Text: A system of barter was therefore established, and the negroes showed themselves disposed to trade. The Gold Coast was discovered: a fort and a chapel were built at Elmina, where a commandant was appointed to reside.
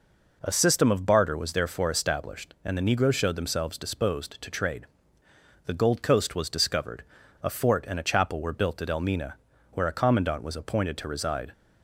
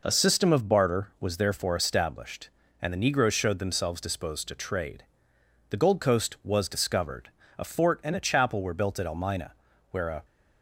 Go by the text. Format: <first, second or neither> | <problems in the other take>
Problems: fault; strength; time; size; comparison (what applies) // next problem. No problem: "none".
first | stops before "commandant was appointed to reside"; at 10.2 s